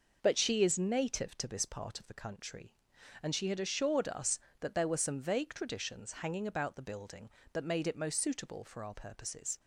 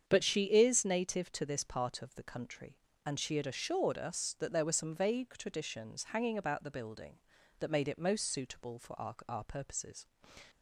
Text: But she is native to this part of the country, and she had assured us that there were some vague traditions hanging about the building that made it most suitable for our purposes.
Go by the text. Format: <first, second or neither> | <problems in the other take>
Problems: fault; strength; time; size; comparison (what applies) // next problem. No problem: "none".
first | starts louder than the rest; strong; until 1.0 s; 7.5 dB // says "our" twice; at 9.2 s